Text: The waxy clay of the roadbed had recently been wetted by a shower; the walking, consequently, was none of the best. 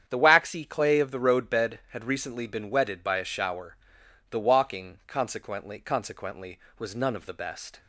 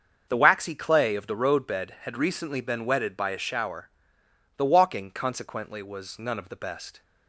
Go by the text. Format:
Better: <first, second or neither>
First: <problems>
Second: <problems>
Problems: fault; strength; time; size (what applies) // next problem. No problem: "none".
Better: second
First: starts louder than the rest; strong; until 1.0 s; 9 dB // says "consequently" twice; at 5.8 s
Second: starts louder than the rest; until 1.3 s; 6.5 dB